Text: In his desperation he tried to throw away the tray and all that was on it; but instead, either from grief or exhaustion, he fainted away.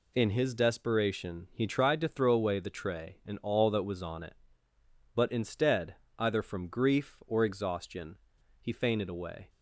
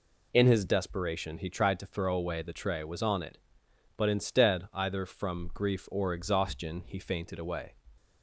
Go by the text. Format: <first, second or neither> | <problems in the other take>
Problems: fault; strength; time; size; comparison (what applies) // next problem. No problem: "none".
first | skips "and all that"; at 2.8 s